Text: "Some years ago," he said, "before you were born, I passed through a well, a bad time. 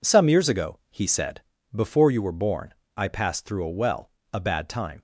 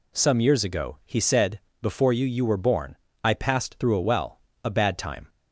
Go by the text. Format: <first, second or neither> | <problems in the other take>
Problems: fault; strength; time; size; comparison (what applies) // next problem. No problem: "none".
first | says "you" twice; at 2.2 s